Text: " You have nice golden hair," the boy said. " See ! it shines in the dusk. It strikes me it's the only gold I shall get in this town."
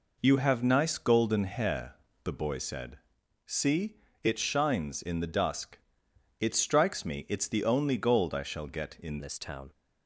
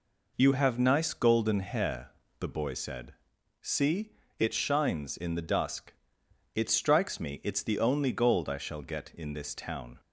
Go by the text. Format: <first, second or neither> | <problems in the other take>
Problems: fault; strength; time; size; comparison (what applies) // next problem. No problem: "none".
second | changes voice at "this"; from 9.1 s on; 0.6 s long